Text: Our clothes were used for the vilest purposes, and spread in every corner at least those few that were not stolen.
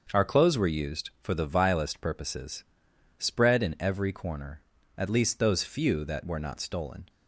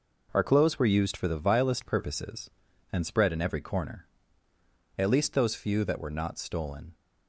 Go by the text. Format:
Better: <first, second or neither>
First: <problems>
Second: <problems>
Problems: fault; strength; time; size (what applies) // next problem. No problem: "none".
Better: second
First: starts louder than the rest; noticeable; until 1.2 s; 6 dB // skips "and"; at 2.9 s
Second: none